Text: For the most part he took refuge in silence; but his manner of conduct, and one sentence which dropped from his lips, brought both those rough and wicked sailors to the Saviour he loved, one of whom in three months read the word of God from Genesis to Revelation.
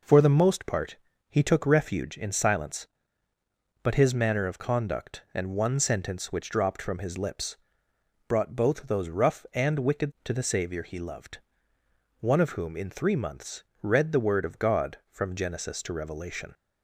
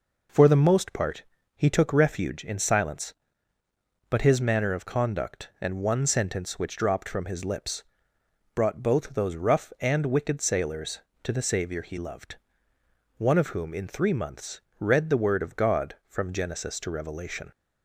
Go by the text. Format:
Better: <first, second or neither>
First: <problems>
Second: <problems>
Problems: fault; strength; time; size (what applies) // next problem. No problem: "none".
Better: second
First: pauses between "part" and "he"; slight; at 0.9 s; 0.32 s long // skips "sailors"; at 10.1 s // pauses between "months" and "read"; slight; at 13.6 s; 0.18 s long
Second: pauses between "part" and "he"; slight; at 1.2 s; 0.32 s long // pauses between "months" and "read"; slight; at 14.6 s; 0.18 s long